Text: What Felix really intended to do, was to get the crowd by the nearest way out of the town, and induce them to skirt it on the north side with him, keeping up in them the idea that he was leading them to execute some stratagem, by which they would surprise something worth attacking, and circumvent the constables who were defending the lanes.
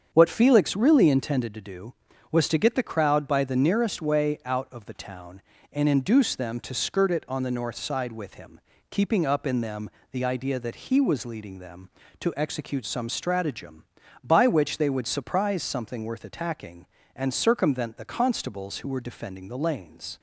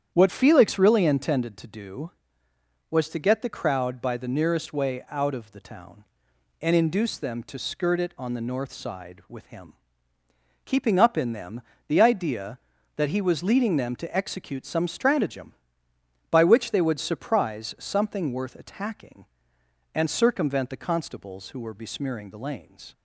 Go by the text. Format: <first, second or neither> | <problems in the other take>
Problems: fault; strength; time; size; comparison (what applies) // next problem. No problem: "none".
first | starts louder than the rest; strong; until 1.1 s; 9.5 dB; strong in the first // pauses between "them" and "the"; slight; at 11.6 s; 0.24 s long; slight in the first // says "besmearing" for "defending"; at 21.7 s